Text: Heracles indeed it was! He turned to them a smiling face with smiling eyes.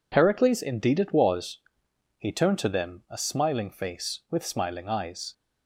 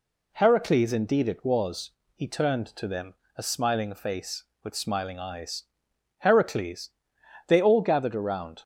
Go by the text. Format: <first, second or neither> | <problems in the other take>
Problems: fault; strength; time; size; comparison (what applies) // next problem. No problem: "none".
first | pauses between "them" and "a"; slight; at 3.1 s; 0.20 s long // goes on to say "Heracles They all gathered around"; strong; from 6.1 s on; 2.4 s long